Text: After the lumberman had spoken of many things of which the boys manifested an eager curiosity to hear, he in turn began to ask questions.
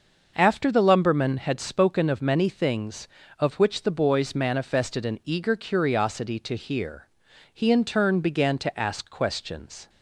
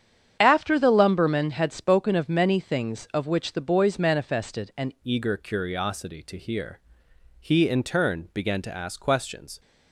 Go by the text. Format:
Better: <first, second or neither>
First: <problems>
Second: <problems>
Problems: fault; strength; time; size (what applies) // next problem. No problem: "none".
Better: first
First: starts louder than the rest; until 1.3 s; 6 dB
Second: starts louder than the rest; strong; until 1.4 s; 8.5 dB // changes voice at "eager"; from 5.0 s on; 4.5 s long